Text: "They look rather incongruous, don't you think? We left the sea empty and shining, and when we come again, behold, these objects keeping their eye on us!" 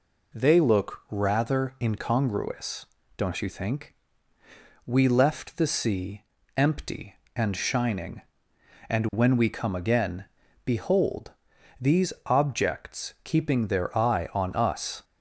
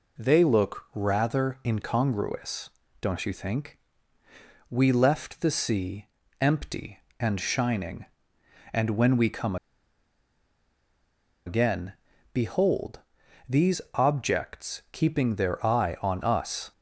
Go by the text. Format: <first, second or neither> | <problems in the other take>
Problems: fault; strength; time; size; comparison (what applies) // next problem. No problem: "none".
first | pauses between "sea" and "empty"; slight; at 6.0 s; 0.34 s long; slight in the first // pauses between "come" and "again"; strong; at 9.5 s; 1.9 s long